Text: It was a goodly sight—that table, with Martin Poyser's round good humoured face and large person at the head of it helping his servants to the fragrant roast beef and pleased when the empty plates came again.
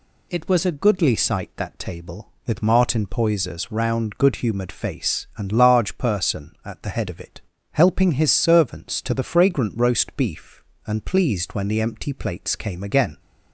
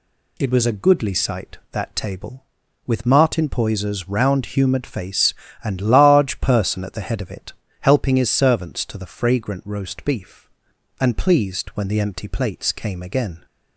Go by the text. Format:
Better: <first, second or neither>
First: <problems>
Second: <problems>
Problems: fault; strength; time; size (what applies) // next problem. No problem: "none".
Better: first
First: pauses between "it" and "helping"; slight; at 7.4 s; 0.32 s long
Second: skips "good"; at 4.4 s // pauses between "it" and "helping"; slight; at 7.5 s; 0.28 s long